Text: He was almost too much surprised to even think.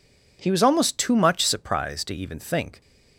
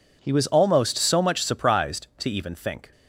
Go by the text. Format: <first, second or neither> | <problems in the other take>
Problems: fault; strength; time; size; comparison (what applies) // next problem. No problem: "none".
first | says "so" for "too"; at 0.9 s